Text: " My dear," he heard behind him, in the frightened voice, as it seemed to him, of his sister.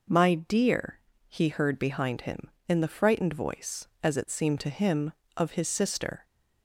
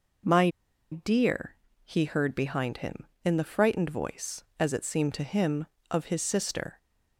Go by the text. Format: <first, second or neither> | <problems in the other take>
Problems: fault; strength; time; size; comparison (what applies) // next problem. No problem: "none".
first | pauses between "My" and "dear"; at 0.4 s; 0.43 s long